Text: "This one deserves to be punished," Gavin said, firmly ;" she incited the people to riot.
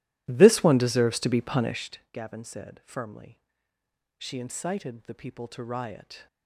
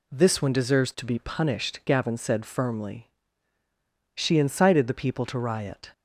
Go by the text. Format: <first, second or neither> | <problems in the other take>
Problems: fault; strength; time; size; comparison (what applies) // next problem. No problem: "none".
second | starts louder than the rest; strong; until 1.9 s; 15.5 dB